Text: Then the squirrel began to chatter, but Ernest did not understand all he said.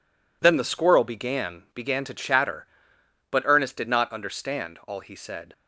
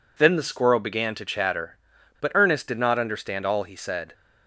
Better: second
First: says "began" twice; at 1.7 s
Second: none

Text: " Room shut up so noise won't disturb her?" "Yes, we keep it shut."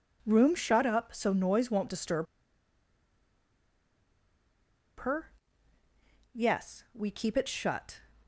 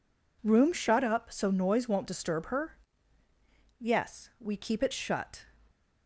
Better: second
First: pauses between "disturb" and "her"; strong; at 2.2 s; 2.7 s long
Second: none

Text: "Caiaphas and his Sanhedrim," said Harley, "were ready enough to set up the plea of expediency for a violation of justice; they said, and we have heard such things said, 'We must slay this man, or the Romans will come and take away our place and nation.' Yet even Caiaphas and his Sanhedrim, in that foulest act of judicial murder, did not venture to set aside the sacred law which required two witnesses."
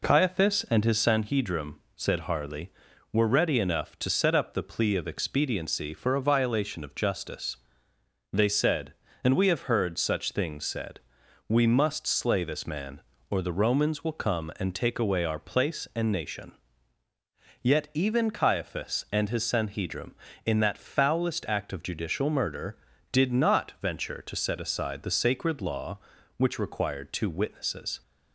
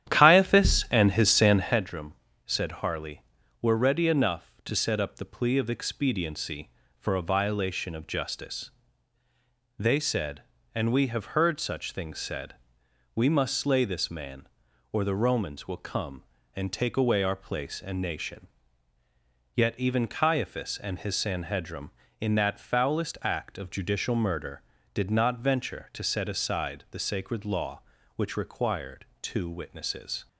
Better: first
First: none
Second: starts louder than the rest; strong; until 1.9 s; 10.5 dB

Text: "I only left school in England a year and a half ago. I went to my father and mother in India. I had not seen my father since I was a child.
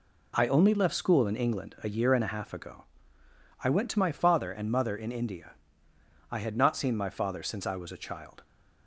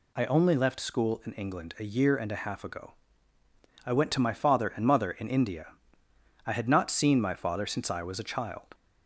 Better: neither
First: none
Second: none

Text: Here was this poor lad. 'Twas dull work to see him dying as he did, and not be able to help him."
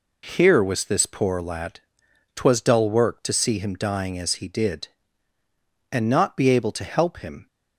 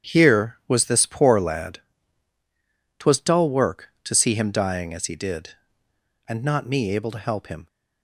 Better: first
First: none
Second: starts louder than the rest; strong; until 1.1 s; 8.5 dB // says "me" for "be"; at 6.6 s

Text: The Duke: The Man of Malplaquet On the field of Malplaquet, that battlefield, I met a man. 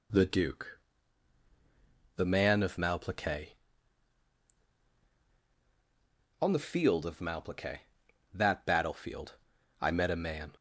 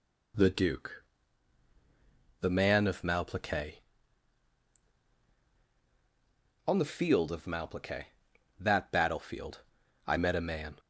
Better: neither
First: none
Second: none

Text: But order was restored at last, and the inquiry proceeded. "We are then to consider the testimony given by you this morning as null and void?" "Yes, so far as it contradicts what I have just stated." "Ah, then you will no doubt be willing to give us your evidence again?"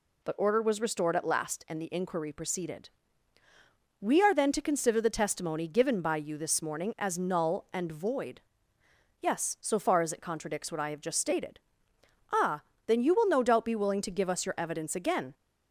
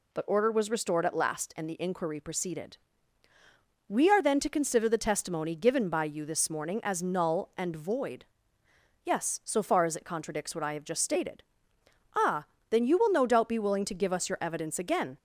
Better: neither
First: none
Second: none

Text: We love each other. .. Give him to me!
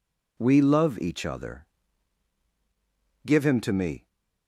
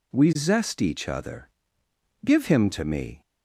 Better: first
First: none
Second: says "zest" for "love"; at 0.3 s

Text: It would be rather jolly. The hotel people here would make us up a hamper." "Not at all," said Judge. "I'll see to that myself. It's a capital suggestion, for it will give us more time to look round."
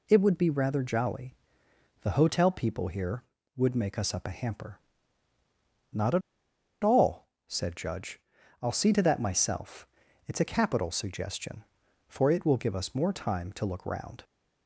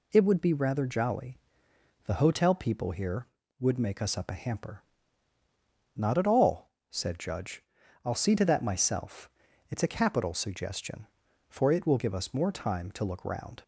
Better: second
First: pauses between "at" and "all"; noticeable; at 6.2 s; 0.62 s long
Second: none

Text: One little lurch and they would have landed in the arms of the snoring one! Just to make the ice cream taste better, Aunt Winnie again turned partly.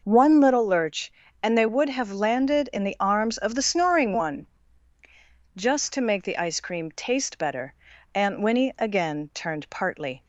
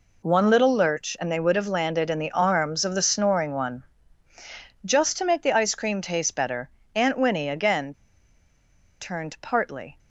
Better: first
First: none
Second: pauses between "again" and "turned"; at 7.9 s; 1.0 s long

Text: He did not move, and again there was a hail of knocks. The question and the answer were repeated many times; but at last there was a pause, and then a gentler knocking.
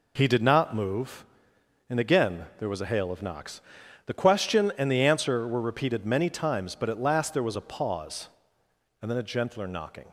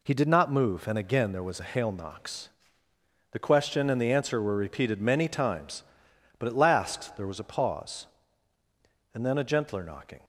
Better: first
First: none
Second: skips "of"; at 1.9 s

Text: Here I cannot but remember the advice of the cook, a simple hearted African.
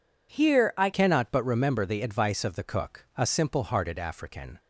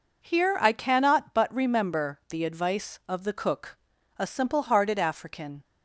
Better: second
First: changes voice at "cannot"; from 0.9 s on; 3.6 s long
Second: none

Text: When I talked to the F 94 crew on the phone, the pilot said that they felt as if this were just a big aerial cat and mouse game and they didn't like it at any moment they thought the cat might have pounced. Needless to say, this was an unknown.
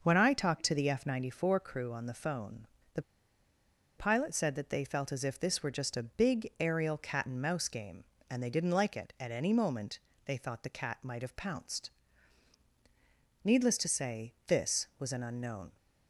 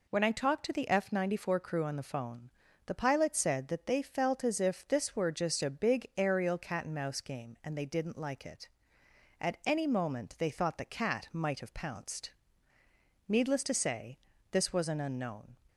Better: second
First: pauses between "the" and "pilot"; noticeable; at 3.0 s; 0.94 s long // pauses between "moment" and "they"; slight; at 9.9 s; 0.26 s long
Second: none

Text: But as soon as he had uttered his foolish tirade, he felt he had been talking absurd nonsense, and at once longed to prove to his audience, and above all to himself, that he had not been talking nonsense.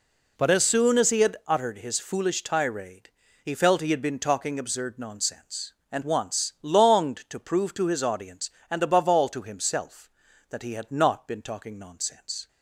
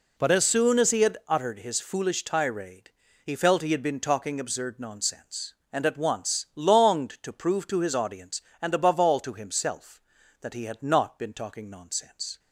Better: second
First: skips "at"; at 6.0 s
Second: none

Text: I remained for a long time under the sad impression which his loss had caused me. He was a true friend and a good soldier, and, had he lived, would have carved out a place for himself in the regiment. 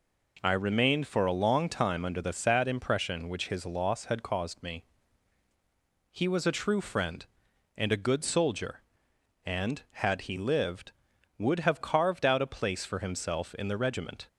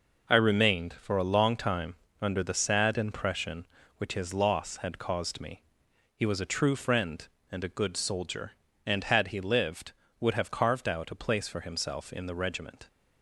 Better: first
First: none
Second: gets quieter; throughout; 6.5 dB // pauses between "time" and "under"; slight; at 1.9 s; 0.26 s long

